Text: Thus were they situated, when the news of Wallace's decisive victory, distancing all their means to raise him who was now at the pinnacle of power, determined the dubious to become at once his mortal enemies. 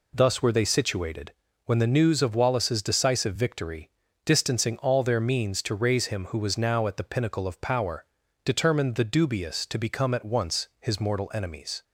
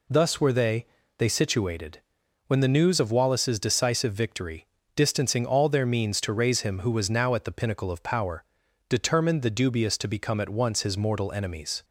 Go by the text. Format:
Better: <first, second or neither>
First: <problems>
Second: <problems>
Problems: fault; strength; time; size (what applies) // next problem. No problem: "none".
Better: first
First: none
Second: says "they" twice; at 1.1 s